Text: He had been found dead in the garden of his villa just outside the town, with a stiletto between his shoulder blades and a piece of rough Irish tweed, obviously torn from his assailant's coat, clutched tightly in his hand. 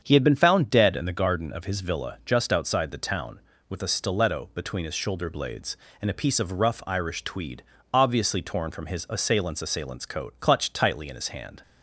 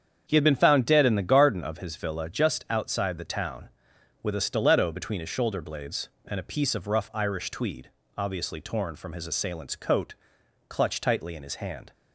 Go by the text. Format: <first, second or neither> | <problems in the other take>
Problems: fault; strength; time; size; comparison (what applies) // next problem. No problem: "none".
second | starts louder than the rest; strong; until 1.0 s; 7.5 dB; strong in the second // says "assailant's" twice; at 9.6 s